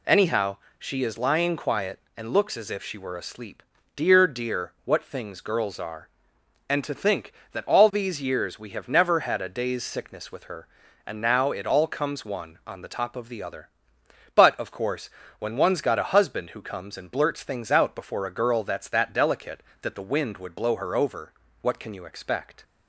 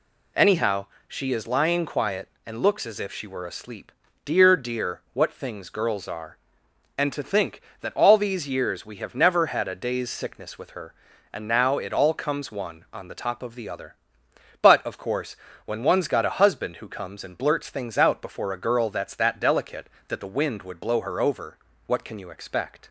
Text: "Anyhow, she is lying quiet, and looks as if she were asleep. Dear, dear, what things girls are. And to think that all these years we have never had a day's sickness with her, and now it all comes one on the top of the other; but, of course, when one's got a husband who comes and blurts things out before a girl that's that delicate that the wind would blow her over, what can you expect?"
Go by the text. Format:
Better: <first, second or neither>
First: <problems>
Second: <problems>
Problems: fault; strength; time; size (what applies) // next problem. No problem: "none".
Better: neither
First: none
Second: none